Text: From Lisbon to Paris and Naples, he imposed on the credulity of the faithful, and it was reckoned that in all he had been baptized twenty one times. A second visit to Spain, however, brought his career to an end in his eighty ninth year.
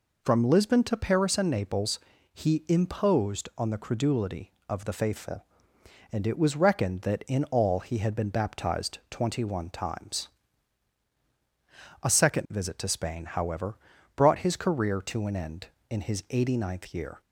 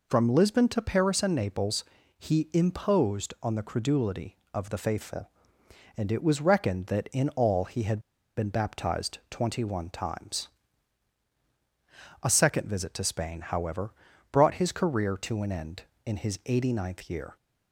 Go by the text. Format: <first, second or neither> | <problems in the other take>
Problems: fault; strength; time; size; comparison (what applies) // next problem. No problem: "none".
first | pauses between "had" and "been"; at 7.9 s; 0.38 s long